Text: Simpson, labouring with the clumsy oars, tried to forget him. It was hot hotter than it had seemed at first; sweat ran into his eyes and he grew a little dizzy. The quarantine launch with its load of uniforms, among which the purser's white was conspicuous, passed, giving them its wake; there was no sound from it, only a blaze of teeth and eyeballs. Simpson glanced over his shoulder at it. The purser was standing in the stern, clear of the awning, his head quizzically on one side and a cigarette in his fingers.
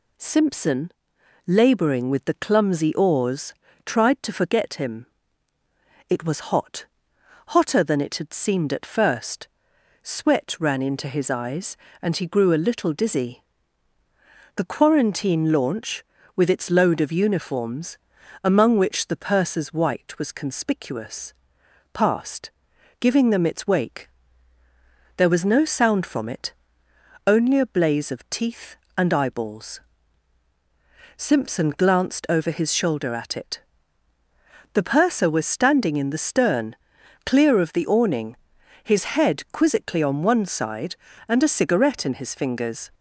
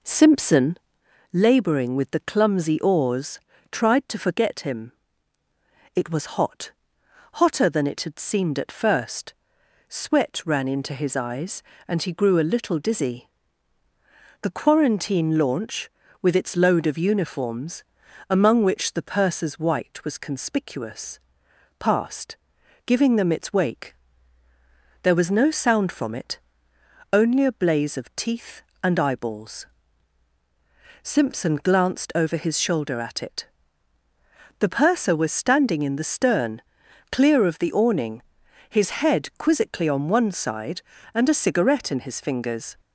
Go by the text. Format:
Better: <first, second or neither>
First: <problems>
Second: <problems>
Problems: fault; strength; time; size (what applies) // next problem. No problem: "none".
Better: first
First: pauses between "hot" and "hotter"; noticeable; at 6.8 s; 0.64 s long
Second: starts louder than the rest; noticeable; until 1.1 s; 4.5 dB // pauses between "hot" and "hotter"; noticeable; at 6.7 s; 0.64 s long